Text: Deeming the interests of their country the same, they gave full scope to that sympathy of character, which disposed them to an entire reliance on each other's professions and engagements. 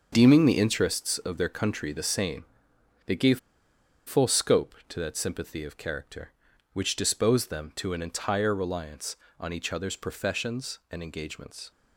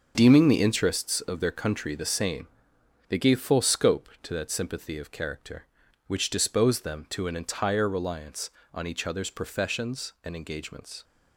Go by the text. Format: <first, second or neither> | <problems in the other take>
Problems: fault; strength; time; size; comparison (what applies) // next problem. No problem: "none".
second | starts louder than the rest; noticeable; until 1.1 s; 6 dB; noticeable in the second // pauses between "gave" and "full"; noticeable; at 3.3 s; 0.67 s long